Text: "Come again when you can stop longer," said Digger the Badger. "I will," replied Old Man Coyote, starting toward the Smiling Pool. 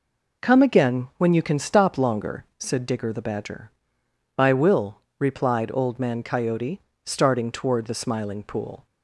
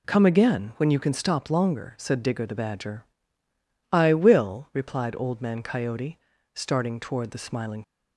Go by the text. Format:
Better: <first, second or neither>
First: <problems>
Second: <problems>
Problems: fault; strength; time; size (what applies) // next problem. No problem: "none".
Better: first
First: none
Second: stops before "Pool"; at 7.8 s